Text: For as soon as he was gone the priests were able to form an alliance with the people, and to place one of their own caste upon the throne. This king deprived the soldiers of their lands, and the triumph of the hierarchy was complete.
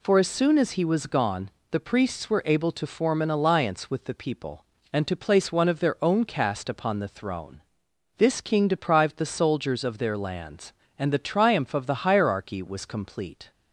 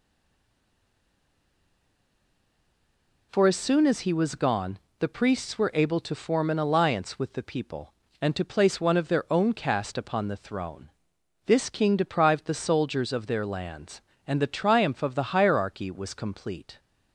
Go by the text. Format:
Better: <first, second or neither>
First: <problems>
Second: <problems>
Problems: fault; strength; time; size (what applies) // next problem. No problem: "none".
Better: first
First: pauses between "gone" and "the"; slight; at 1.5 s; 0.20 s long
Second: stays silent before the first word; strong; until 3.3 s; 3.3 s long // pauses between "gone" and "the"; slight; at 4.7 s; 0.20 s long